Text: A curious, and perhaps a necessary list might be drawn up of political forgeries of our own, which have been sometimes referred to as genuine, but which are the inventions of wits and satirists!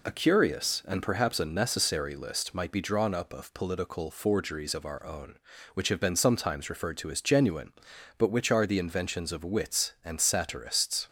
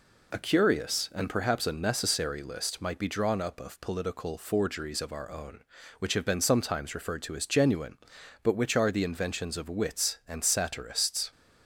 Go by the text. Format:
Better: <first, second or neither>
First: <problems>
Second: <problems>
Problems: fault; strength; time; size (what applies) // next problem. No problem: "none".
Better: neither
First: none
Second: none